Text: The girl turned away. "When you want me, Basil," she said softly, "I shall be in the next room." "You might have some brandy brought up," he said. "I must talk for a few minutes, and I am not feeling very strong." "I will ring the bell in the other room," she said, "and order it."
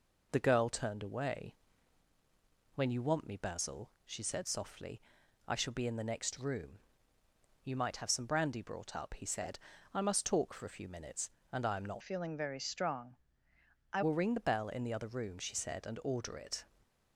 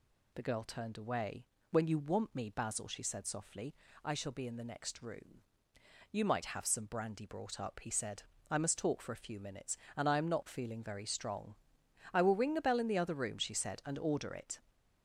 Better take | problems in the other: second | changes voice from "feeling" to "I"; from 12.0 to 14.0 s; 2.0 s long // stays silent after the last word; slight; from 16.6 s on; 0.5 s long

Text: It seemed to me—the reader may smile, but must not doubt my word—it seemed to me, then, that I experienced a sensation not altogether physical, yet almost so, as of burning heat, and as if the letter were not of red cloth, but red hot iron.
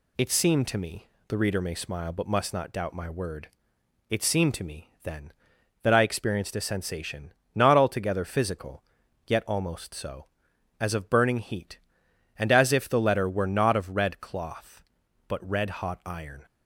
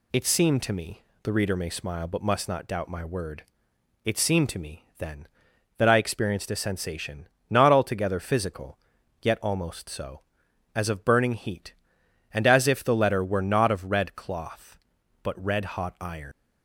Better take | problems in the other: first | pauses between "sensation" and "not"; slight; at 7.2 s; 0.24 s long; slight in the first // leaves "iron" unfinished; at 16.3 s; 85 ms

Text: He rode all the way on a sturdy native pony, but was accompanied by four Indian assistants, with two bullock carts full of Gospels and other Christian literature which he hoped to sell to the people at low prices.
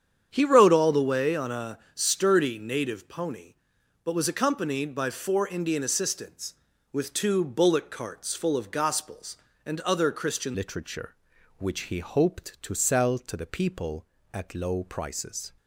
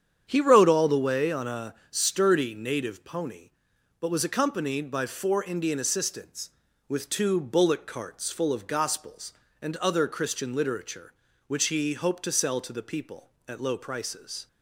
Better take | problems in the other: second | starts louder than the rest; strong; until 1.3 s; 8.5 dB; strong in the second // pauses between "a" and "sturdy"; slight; at 1.7 s; 0.16 s long; slight in the second // changes voice at "literature"; from 10.5 s on; 5.0 s long

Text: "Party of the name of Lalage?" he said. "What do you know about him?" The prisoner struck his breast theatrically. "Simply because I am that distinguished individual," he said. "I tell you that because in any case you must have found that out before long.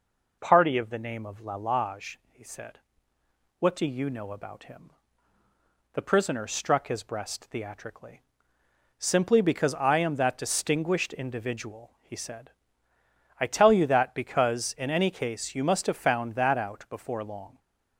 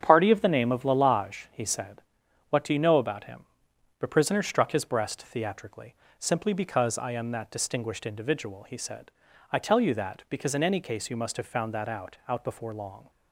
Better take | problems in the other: first | starts louder than the rest; strong; until 1.0 s; 7.5 dB // says "out" twice; at 12.2 s

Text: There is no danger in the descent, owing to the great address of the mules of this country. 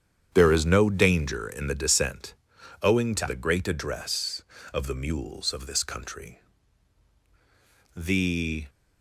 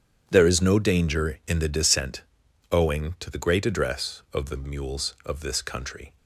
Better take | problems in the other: second | starts louder than the rest; strong; until 1.3 s; 8.5 dB; strong in the second // goes on to say "The"; noticeable; from 7.9 s on; 0.72 s long

